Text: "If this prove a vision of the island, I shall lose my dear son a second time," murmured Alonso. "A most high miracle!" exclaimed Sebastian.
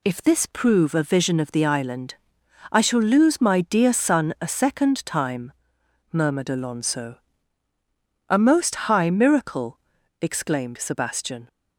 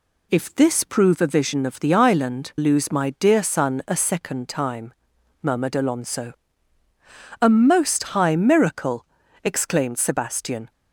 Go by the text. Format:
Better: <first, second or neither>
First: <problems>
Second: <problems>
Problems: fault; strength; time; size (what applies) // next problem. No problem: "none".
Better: first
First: none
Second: skips "I shall"; at 2.5 s